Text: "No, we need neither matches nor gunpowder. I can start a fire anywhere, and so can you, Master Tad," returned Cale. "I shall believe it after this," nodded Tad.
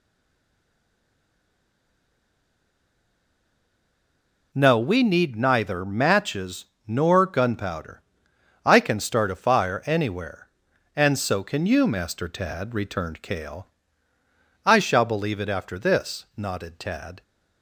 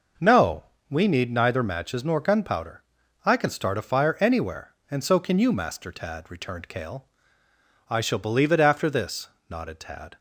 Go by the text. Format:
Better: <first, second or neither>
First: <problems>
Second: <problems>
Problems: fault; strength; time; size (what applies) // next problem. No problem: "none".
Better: second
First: stays silent before the first word; strong; until 4.5 s; 4.5 s long // pauses between "matches" and "nor"; slight; at 6.6 s; 0.20 s long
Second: none